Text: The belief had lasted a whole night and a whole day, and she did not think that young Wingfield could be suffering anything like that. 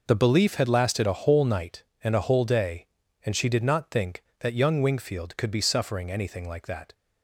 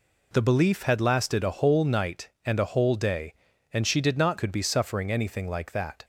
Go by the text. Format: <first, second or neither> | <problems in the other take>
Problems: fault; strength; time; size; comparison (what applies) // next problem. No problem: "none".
first | skips "think that young Wingfield"; at 4.3 s